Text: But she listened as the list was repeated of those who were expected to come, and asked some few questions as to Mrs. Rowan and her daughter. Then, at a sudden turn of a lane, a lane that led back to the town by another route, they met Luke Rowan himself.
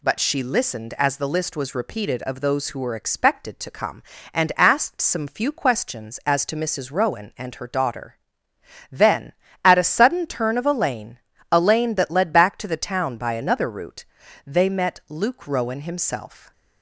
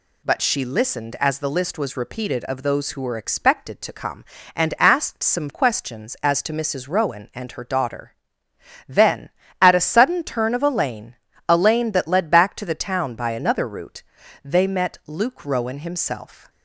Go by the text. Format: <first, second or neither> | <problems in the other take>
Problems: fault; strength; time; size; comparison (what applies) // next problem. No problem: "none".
first | skips "few"; at 5.4 s